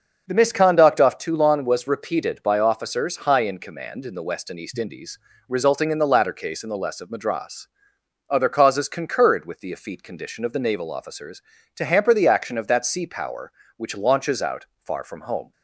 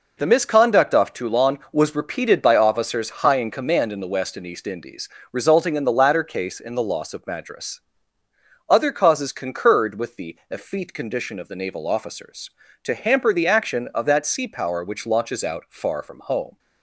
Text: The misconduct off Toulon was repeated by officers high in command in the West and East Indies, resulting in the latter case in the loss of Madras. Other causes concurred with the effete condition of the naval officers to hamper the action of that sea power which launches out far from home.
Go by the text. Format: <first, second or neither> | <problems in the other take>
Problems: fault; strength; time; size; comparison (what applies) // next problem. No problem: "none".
second | starts louder than the rest; until 1.2 s; 6.5 dB // says "less" for "loss"; at 6.7 s